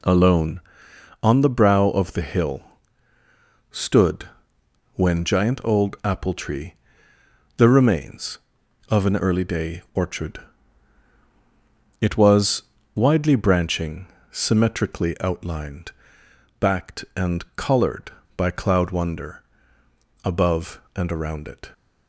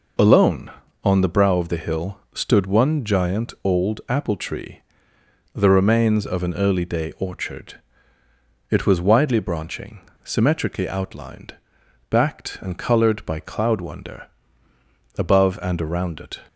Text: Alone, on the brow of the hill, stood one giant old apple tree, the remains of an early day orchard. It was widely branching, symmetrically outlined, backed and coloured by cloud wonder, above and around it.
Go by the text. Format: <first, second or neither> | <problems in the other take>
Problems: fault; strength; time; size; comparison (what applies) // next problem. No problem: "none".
second | says "when" for "one"; at 4.9 s // pauses between "was" and "widely"; slight; at 12.6 s; 0.32 s long